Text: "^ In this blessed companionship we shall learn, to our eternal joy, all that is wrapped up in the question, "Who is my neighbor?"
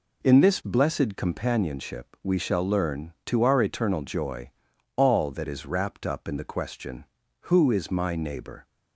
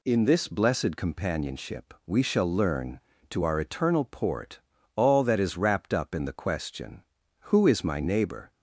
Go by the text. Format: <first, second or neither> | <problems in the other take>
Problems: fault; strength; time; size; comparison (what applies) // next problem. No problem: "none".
first | says "port" for "joy"; at 4.0 s